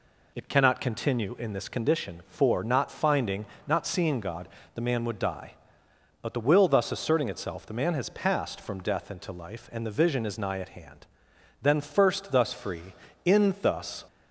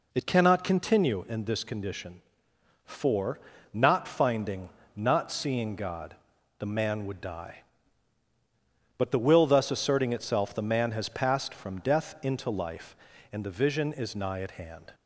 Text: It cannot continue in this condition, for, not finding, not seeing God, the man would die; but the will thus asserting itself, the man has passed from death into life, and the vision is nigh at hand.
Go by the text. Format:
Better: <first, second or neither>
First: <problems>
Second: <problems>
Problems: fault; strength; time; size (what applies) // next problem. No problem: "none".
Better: second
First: goes on to say "Then first thus free in thus"; strong; from 11.6 s on; 2.4 s long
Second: none